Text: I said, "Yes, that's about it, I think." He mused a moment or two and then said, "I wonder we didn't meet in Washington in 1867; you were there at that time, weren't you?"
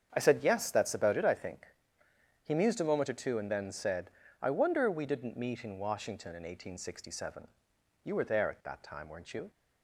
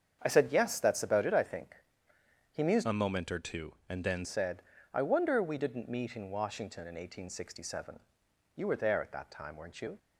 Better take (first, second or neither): first